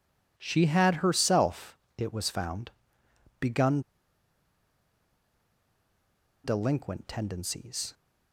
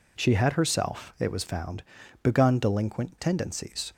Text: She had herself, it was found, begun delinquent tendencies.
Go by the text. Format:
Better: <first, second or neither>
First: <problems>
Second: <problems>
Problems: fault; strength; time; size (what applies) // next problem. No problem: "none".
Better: second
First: pauses between "begun" and "delinquent"; strong; at 3.8 s; 2.6 s long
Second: none